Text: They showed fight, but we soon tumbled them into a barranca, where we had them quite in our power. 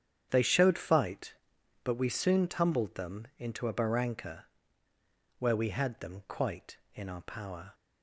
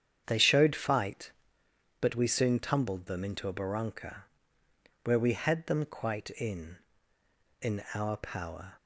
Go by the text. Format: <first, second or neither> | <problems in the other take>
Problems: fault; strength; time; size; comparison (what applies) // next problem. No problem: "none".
first | starts louder than the rest; strong; until 1.2 s; 8.5 dB; strong in the first // says "in" twice; at 7.6 s